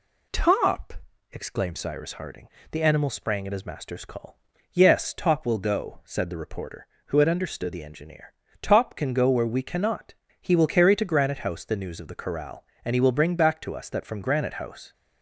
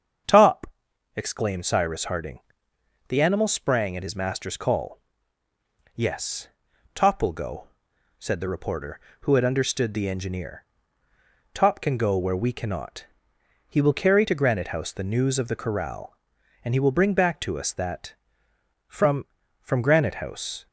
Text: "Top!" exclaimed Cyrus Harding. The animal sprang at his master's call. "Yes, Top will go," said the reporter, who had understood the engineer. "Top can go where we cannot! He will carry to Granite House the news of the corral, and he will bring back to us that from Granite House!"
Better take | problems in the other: first | starts louder than the rest; strong; until 1.7 s; 7.5 dB // says "from" twice; at 19.6 s

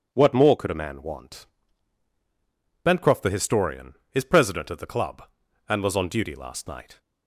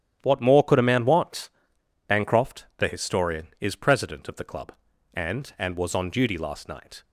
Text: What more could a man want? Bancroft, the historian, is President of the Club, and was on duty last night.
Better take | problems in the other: first | starts louder than the rest; strong; until 1.2 s; 11 dB // says "and" twice; at 5.5 s

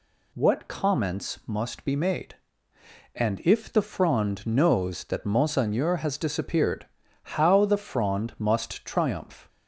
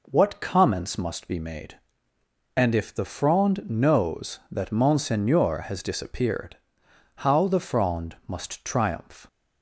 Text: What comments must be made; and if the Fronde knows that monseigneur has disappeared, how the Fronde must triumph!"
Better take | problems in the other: neither | none

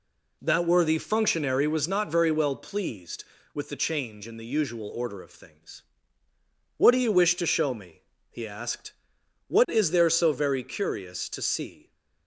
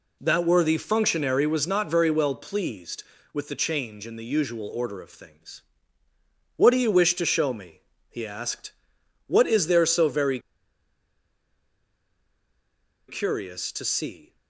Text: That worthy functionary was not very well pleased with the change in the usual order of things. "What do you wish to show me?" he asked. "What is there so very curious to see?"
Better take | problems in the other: first | pauses between "very" and "curious"; strong; at 10.4 s; 2.6 s long

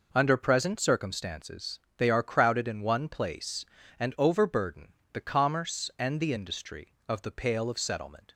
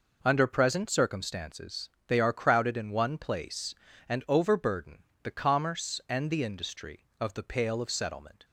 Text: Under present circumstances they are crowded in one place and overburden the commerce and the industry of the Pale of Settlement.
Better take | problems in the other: neither | pauses between "circumstances" and "they"; slight; the same in both // pauses between "overburden" and "the"; slight; the same in both

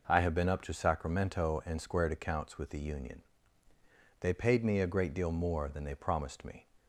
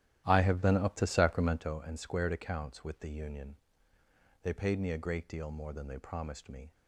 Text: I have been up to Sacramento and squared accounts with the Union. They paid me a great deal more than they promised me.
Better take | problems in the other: first | starts louder than the rest; strong; until 1.8 s; 12.5 dB

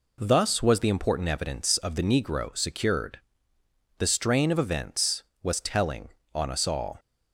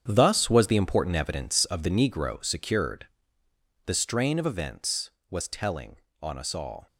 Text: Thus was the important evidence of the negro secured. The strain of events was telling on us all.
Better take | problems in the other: first | gets quieter; strong; throughout; 9.5 dB

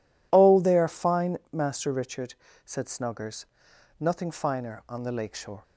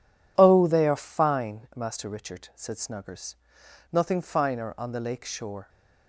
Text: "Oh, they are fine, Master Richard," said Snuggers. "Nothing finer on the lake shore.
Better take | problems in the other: neither | none

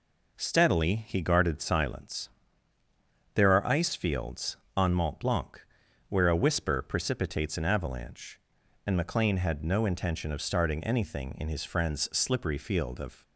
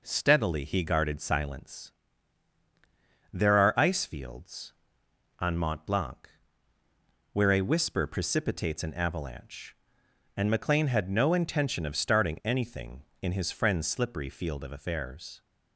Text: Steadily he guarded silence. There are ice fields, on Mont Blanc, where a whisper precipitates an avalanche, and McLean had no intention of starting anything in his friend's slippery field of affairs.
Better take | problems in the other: second | stops before "affairs"; at 13.2 s

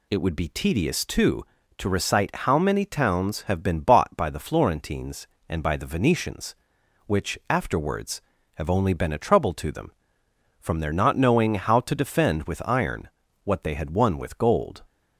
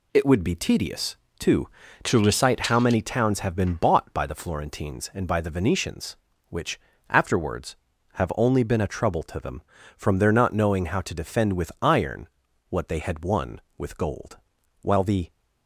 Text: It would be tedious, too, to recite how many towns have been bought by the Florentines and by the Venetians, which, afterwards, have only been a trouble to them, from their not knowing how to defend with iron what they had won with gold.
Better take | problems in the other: first | pauses between "iron" and "what"; at 12.2 s; 0.42 s long; slight in the first // goes on to say "While the"; slight; from 14.8 s on; 0.48 s long

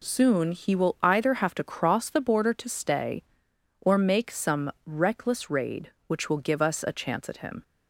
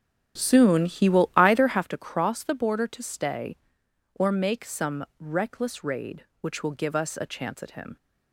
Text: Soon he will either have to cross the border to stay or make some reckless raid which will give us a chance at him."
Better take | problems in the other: first | starts louder than the rest; strong; until 1.9 s; 9 dB

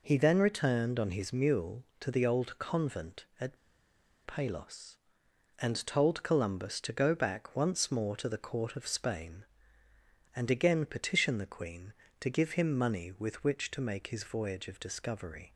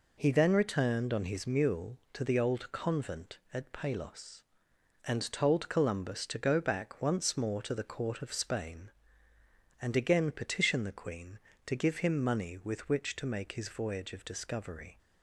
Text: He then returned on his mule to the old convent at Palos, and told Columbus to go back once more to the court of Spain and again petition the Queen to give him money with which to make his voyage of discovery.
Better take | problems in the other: second | pauses between "at" and "Palos"; noticeable; at 3.5 s; 0.68 s long

